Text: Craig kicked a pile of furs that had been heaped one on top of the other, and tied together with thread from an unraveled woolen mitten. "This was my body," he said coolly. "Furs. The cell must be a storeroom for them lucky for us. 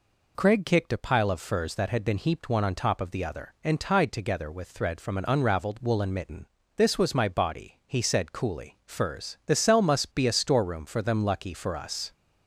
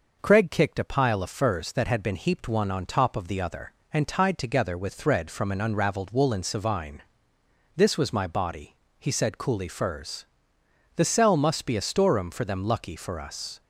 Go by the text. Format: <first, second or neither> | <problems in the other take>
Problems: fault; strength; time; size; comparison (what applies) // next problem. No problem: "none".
first | says "savine" for "mitten"; at 6.4 s